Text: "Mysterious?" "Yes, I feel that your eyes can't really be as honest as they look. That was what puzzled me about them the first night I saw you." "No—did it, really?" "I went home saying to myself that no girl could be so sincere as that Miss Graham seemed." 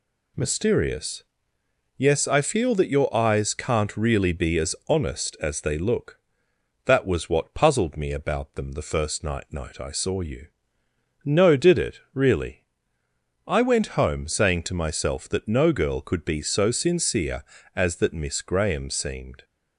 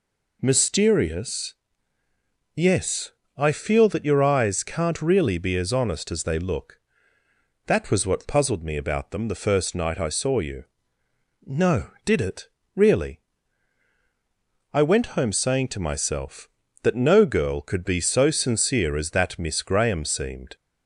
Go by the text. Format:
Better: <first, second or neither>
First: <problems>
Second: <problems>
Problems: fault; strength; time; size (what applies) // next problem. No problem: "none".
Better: second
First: says "night" twice; at 9.5 s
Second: none